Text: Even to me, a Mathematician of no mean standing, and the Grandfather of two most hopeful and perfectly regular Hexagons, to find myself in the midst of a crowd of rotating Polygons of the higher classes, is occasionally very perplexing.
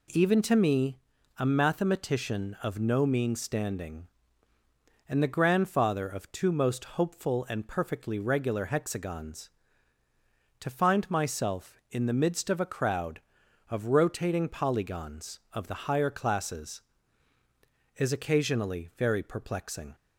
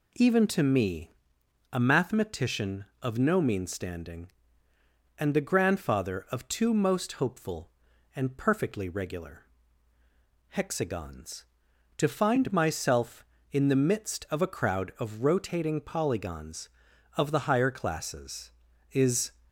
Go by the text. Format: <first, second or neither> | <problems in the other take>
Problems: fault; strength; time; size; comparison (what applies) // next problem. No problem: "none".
first | pauses between "regular" and "Hexagons"; at 9.4 s; 1.0 s long // stops before "occasionally very perplexing"; at 19.4 s